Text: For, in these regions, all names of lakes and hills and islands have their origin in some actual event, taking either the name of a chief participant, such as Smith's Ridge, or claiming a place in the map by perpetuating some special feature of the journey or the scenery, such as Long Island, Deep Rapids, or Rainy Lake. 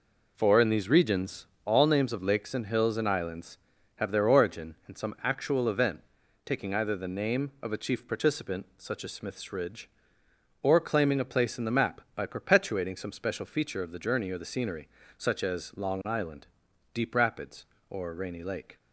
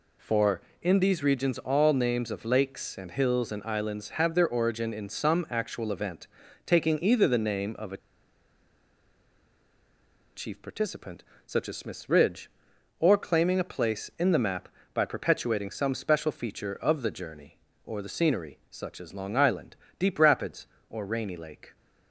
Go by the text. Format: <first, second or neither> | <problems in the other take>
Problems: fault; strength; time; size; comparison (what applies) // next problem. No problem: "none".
first | pauses between "a" and "chief"; strong; at 7.9 s; 2.3 s long